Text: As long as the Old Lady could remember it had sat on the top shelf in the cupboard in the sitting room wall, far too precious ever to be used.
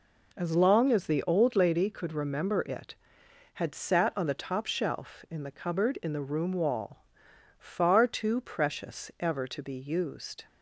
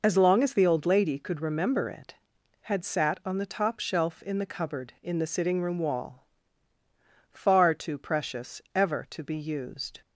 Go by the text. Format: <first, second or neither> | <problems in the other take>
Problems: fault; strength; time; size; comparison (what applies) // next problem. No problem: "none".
second | skips "sitting"; at 6.2 s